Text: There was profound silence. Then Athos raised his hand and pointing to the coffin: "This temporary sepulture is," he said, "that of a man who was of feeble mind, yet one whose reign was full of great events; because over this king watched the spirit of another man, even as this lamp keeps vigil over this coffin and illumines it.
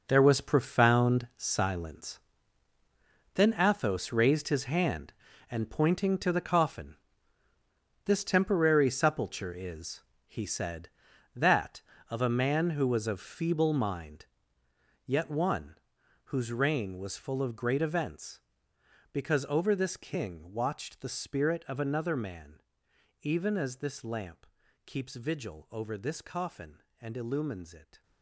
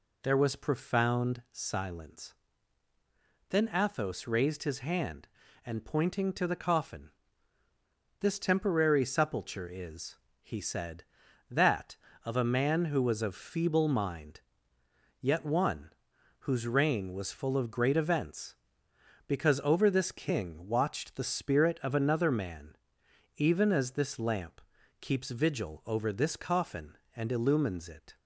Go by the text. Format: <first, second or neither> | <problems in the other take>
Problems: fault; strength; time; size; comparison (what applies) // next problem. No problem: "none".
second | gets quieter; strong; throughout; 11.5 dB // pauses between "one" and "whose"; noticeable; at 15.7 s; 0.50 s long; noticeable in the second // pauses between "lamp" and "keeps"; at 24.4 s; 0.40 s long; also in the second